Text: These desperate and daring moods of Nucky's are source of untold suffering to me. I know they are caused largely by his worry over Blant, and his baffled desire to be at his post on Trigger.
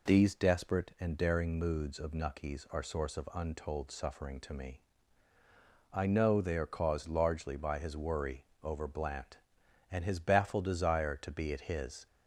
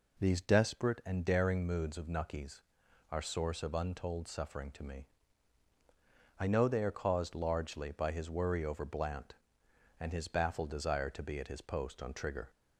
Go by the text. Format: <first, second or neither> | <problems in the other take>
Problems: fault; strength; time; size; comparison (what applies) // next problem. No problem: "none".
second | pauses between "worry" and "over"; slight; at 8.4 s; 0.18 s long // stops before "post on Trigger"; at 12.0 s